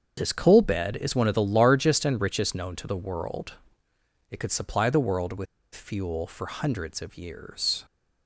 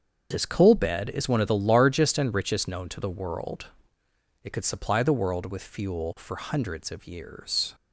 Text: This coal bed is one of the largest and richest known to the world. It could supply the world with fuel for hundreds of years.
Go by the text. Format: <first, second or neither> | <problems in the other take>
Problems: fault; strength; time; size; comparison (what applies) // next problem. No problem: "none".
second | starts louder than the rest; until 1.1 s; 7 dB; also in the second // pauses between "with" and "fuel"; slight; at 5.4 s; 0.29 s long